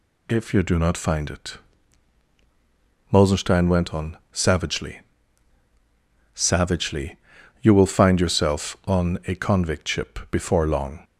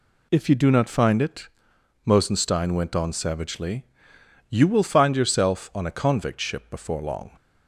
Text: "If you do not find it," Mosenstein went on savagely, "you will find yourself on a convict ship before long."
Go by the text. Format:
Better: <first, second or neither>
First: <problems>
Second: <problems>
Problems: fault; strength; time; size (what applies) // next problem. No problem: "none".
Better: second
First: says "savagely" twice; at 6.3 s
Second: none